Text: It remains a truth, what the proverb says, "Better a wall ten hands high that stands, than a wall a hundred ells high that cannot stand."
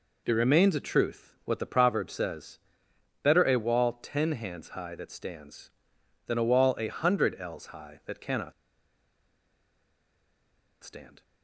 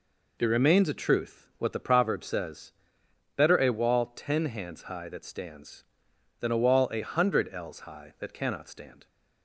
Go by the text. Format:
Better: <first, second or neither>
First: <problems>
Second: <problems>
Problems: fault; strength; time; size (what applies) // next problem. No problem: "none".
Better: second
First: pauses between "cannot" and "stand"; strong; at 8.5 s; 2.3 s long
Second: none